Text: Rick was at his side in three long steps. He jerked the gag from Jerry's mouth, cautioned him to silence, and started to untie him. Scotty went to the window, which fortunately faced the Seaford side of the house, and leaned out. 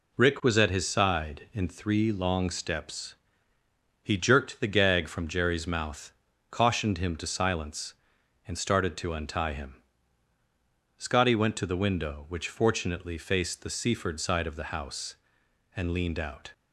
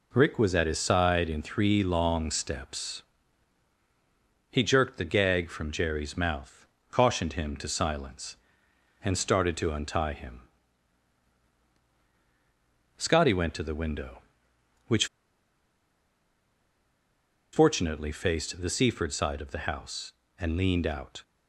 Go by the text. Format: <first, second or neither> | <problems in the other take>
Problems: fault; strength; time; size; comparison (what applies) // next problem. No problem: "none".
first | pauses between "which" and "fortunately"; strong; at 15.0 s; 2.4 s long